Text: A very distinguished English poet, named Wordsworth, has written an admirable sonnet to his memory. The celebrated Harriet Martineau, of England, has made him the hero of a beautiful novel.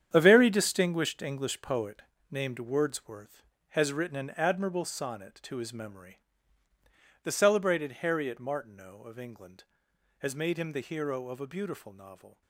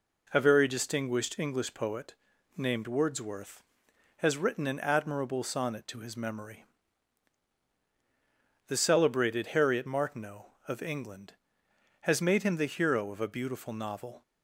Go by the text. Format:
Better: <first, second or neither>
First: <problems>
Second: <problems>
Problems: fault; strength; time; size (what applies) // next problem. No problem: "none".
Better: second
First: gets quieter; strong; throughout; 11 dB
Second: none